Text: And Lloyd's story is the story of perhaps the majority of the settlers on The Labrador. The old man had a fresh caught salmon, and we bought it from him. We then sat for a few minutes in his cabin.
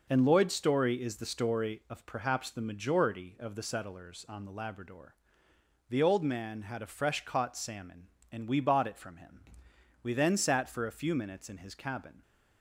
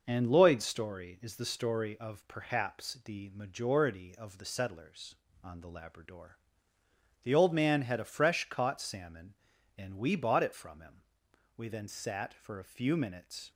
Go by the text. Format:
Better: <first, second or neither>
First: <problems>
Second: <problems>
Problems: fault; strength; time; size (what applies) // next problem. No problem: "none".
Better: first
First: none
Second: stops before "in his cabin"; at 13.5 s